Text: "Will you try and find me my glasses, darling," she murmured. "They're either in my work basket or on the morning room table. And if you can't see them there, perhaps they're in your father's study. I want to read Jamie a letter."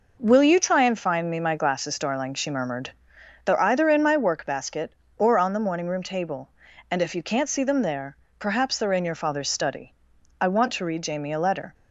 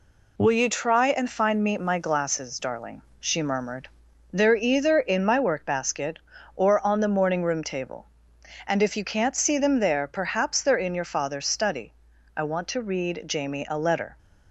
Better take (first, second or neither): neither